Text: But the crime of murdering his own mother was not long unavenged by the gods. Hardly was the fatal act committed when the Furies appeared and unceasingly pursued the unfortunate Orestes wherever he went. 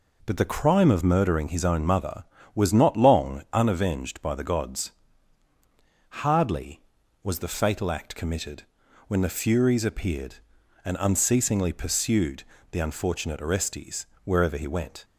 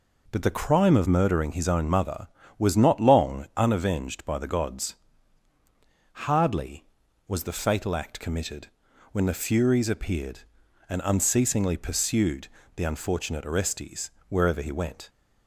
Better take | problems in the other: neither | pauses between "committed" and "when"; the same in both // pauses between "pursued" and "the"; slight; the same in both // pauses between "Orestes" and "wherever"; slight; the same in both

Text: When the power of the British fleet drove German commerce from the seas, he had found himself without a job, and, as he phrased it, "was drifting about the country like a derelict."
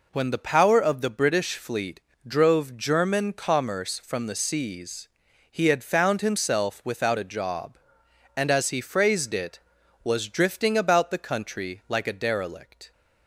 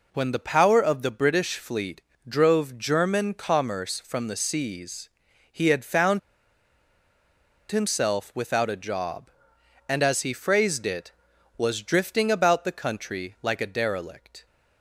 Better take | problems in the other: first | pauses between "fleet" and "drove"; slight; at 2.0 s; 0.28 s long; slight in the first // pauses between "found" and "himself"; strong; at 6.1 s; 1.5 s long

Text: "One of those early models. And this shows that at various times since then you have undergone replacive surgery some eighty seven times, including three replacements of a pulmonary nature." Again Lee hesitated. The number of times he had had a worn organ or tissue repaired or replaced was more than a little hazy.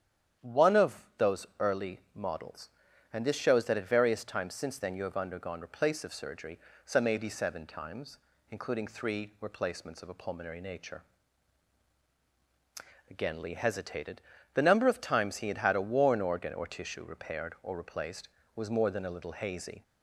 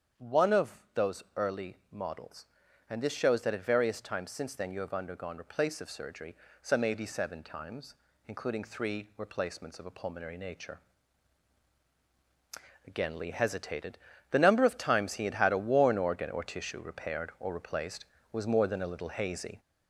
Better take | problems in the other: first | gets louder; throughout; 3.5 dB // starts louder than the rest; strong; until 1.4 s; 8 dB; strong in the first // pauses between "early" and "models"; slight; at 1.7 s; 0.16 s long; slight in the first // pauses between "surgery" and "some"; slight; at 6.3 s; 0.26 s long; slight in the first

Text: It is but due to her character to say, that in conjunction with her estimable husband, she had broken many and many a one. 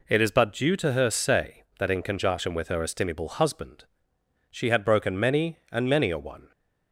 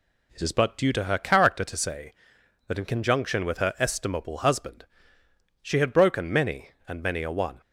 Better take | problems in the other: second | skips "character to"; at 1.0 s

